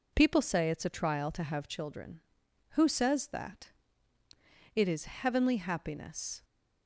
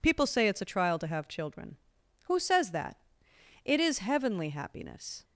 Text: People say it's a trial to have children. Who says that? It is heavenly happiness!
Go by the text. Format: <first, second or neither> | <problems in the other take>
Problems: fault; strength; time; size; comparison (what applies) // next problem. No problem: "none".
neither | none